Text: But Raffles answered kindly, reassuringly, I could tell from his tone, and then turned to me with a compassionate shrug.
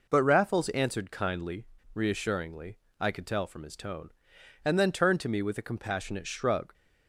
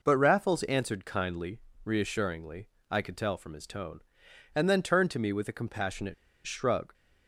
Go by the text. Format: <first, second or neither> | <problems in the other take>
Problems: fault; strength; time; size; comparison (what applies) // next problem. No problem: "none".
first | pauses between "compassionate" and "shrug"; slight; at 6.1 s; 0.32 s long